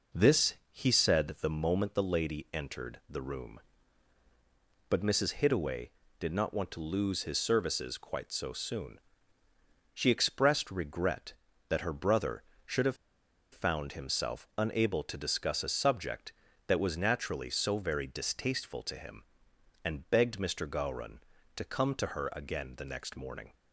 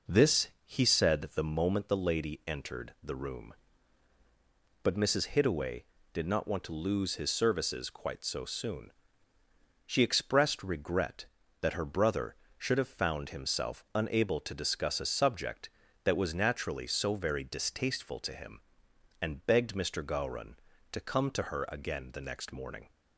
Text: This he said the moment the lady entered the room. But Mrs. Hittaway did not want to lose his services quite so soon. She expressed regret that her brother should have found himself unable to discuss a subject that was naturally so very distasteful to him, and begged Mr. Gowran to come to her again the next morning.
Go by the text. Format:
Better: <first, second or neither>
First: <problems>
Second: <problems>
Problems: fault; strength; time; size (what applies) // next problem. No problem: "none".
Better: second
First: pauses between "This" and "he"; slight; at 0.5 s; 0.16 s long // pauses between "have" and "found"; noticeable; at 12.9 s; 0.55 s long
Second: pauses between "This" and "he"; slight; at 0.4 s; 0.16 s long